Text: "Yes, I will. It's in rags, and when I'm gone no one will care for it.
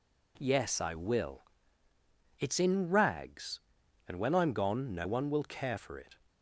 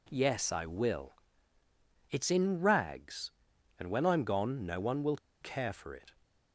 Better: first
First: none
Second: pauses between "will" and "care"; slight; at 5.1 s; 0.23 s long

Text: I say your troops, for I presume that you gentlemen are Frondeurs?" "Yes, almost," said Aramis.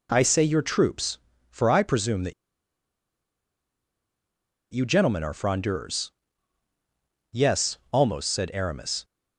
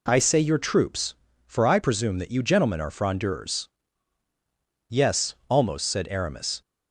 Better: second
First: pauses between "that" and "you"; strong; at 2.3 s; 2.3 s long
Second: none

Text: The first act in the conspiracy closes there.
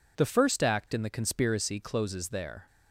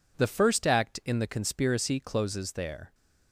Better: neither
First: none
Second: none

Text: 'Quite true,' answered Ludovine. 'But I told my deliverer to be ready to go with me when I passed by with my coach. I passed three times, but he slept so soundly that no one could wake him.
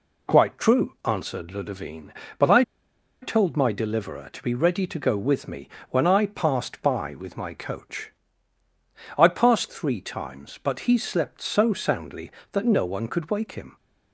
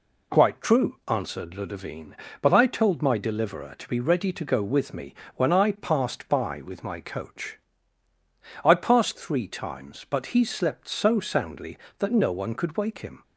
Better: second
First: pauses between "I" and "told"; noticeable; at 2.6 s; 0.59 s long // pauses between "me" and "when"; slight; at 5.6 s; 0.22 s long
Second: pauses between "me" and "when"; slight; at 5.1 s; 0.22 s long

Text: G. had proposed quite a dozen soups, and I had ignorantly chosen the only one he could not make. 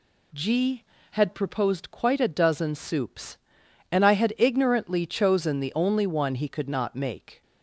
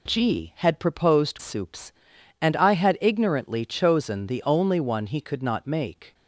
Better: first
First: none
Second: skips "quite a dozen"; at 1.3 s

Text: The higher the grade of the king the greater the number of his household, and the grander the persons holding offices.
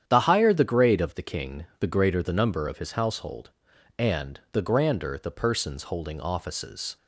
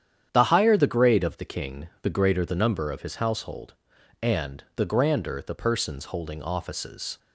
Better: neither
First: starts louder than the rest; strong; until 1.0 s; 9 dB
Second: starts louder than the rest; strong; until 1.3 s; 9 dB

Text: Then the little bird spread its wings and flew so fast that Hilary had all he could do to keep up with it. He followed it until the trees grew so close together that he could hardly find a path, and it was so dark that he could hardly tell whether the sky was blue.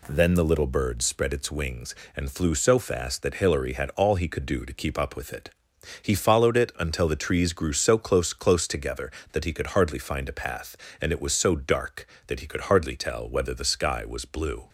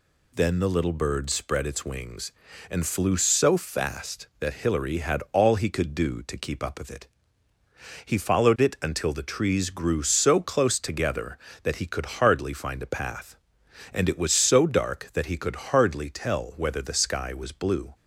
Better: second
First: says "close" twice; at 8.3 s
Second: none

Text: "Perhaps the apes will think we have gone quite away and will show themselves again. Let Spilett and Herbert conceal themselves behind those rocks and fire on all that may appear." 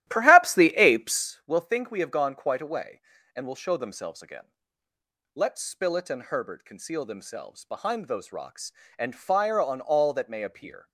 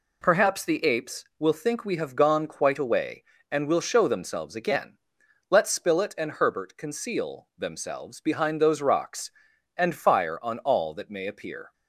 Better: second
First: starts louder than the rest; strong; until 1.3 s; 13.5 dB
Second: none

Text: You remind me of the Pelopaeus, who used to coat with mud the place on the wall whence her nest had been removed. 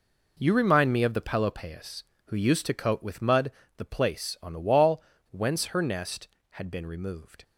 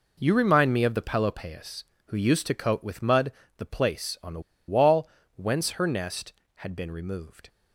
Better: first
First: pauses between "mud" and "the"; slight; at 3.4 s; 0.28 s long // pauses between "wall" and "whence"; slight; at 5.0 s; 0.29 s long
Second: pauses between "mud" and "the"; slight; at 3.3 s; 0.28 s long // pauses between "the" and "wall"; slight; at 4.4 s; 0.27 s long // pauses between "wall" and "whence"; slight; at 5.0 s; 0.28 s long

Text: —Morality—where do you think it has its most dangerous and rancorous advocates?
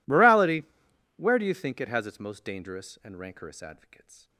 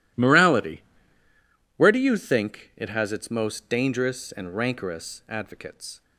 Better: neither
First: none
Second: none

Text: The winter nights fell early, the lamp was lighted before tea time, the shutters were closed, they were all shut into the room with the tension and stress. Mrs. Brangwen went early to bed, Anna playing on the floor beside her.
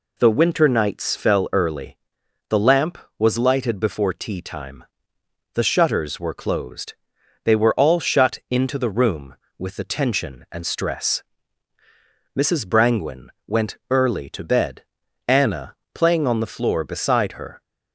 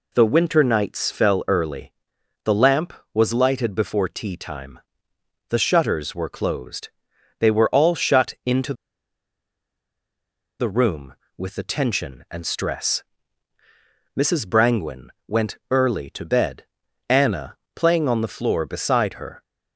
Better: first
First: pauses between "Brangwen" and "went"; slight; at 13.2 s; 0.18 s long // pauses between "Anna" and "playing"; slight; at 15.7 s; 0.20 s long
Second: pauses between "into" and "the"; strong; at 8.7 s; 1.8 s long // pauses between "Brangwen" and "went"; slight; at 15.0 s; 0.18 s long // pauses between "Anna" and "playing"; slight; at 17.5 s; 0.20 s long

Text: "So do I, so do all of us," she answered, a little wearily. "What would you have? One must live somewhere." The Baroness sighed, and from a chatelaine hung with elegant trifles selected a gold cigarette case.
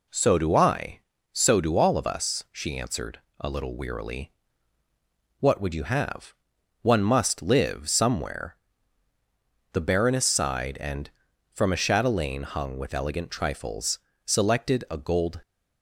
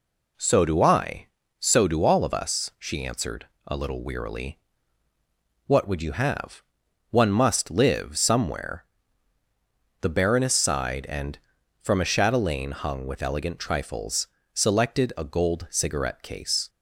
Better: second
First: pauses between "trifles" and "selected"; slight; at 13.9 s; 0.26 s long // stops before "cigarette case"; at 15.4 s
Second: pauses between "trifles" and "selected"; slight; at 14.2 s; 0.26 s long

